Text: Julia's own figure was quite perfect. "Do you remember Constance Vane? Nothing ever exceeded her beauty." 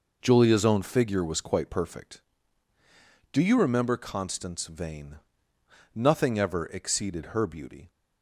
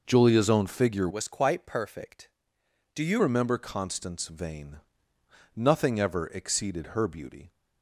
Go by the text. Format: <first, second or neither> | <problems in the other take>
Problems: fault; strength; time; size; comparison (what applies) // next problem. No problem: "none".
first | changes voice from "was" to "you"; from 1.0 to 3.2 s; 2.2 s long